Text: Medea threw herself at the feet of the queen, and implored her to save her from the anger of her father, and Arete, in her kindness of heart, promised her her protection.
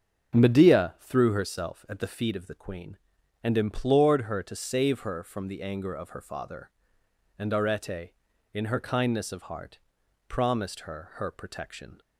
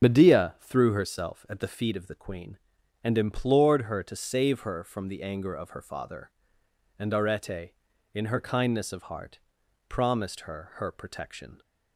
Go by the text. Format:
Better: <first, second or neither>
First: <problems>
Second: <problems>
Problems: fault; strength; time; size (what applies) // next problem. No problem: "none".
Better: first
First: starts louder than the rest; until 1.3 s; 7 dB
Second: loses the start of "Medea"; at 0.0 s; 90 ms // starts louder than the rest; until 1.0 s; 6.5 dB